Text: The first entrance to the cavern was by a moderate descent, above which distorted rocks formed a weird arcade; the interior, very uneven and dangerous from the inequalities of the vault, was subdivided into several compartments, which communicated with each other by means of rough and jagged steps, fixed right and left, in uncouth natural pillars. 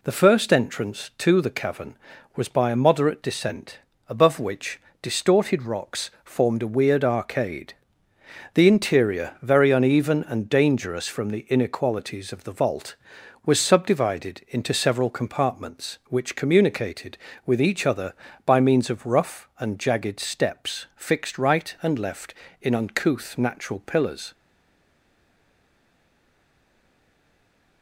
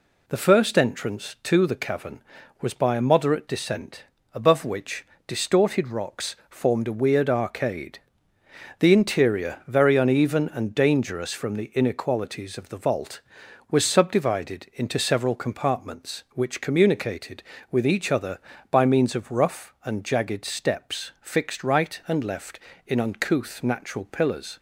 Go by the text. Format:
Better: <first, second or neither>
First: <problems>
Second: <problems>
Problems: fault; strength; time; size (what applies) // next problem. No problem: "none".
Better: second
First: pauses between "which" and "distorted"; slight; at 4.8 s; 0.22 s long // pauses between "rocks" and "formed"; slight; at 6.0 s; 0.16 s long // stays silent after the last word; strong; from 24.3 s on; 3.5 s long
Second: pauses between "which" and "distorted"; slight; at 5.0 s; 0.22 s long // pauses between "rocks" and "formed"; slight; at 6.3 s; 0.16 s long